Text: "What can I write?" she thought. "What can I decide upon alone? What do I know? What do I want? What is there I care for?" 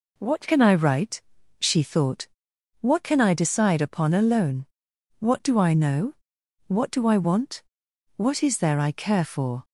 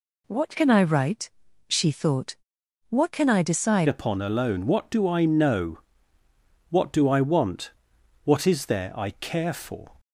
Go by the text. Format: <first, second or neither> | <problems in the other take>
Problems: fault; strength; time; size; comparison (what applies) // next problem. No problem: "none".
first | changes voice at "upon"; from 3.8 s on; 6.1 s long